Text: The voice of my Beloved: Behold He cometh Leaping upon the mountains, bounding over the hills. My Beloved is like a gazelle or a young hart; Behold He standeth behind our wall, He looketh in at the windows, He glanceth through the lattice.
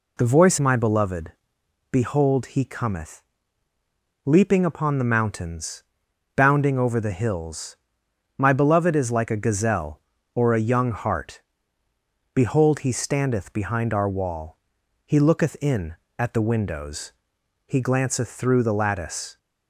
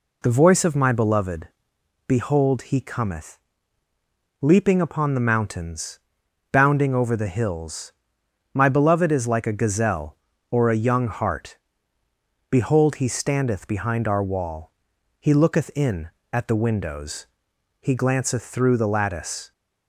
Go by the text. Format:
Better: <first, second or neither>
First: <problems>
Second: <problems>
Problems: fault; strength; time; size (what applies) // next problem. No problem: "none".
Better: second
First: skips "of"; at 0.5 s // pauses between "cometh" and "Leaping"; at 3.2 s; 1.0 s long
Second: pauses between "cometh" and "Leaping"; at 3.3 s; 1.0 s long